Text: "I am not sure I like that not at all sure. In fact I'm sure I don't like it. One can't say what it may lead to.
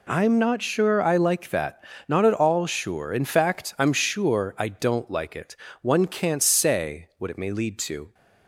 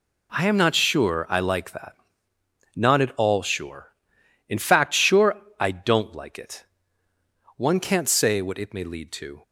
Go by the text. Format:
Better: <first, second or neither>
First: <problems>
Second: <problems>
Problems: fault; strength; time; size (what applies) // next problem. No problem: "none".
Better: first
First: pauses between "that" and "not"; slight; at 1.8 s; 0.24 s long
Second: pauses between "that" and "not"; noticeable; at 1.9 s; 0.76 s long // skips "I'm"; at 4.9 s // pauses between "sure" and "I"; slight; at 5.3 s; 0.24 s long